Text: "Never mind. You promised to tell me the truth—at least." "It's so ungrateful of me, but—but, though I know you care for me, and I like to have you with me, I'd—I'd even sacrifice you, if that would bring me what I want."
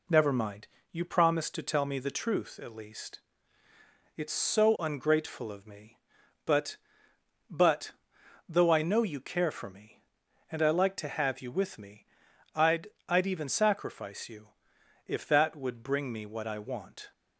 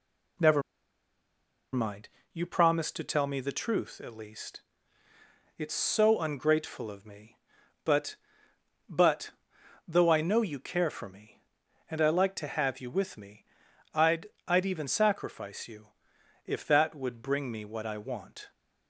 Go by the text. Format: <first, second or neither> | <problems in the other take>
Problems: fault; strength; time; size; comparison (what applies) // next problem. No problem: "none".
first | pauses between "Never" and "mind"; at 0.6 s; 1.1 s long